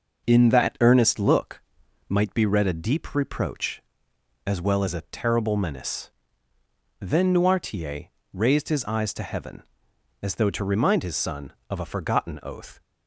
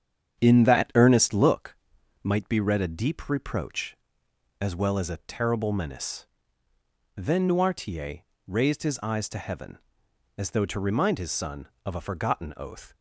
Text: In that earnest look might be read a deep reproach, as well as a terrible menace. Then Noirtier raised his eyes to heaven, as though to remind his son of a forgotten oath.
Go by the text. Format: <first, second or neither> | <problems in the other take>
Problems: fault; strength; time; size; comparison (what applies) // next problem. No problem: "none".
first | starts louder than the rest; strong; until 1.6 s; 8 dB // pauses between "look" and "might"; noticeable; at 1.7 s; 0.46 s long; noticeable in the first // pauses between "Noirtier" and "raised"; slight; at 8.1 s; 0.26 s long; slight in the first